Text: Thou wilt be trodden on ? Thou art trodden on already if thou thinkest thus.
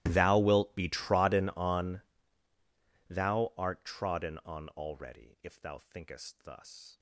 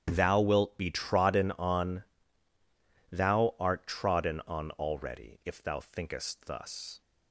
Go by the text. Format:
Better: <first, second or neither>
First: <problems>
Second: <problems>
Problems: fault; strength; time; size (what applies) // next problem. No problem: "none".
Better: second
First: gets quieter; strong; throughout; 25.5 dB // starts louder than the rest; strong; until 1.0 s; 16.5 dB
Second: starts louder than the rest; strong; until 1.0 s; 9.5 dB